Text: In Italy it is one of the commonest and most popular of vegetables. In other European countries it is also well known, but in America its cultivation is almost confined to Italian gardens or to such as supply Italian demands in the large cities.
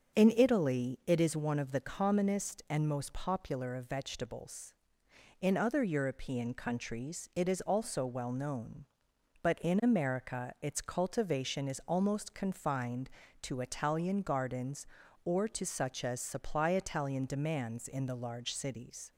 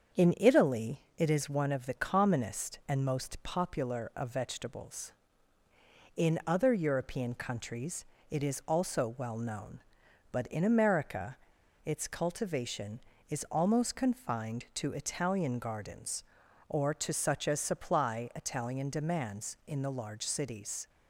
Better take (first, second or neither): first